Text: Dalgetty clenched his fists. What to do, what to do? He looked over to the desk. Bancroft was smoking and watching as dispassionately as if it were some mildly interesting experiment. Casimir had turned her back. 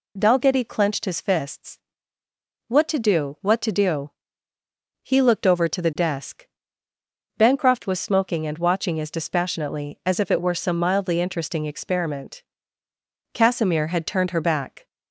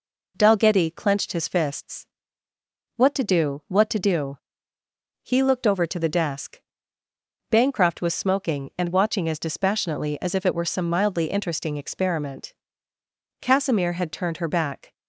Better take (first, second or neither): neither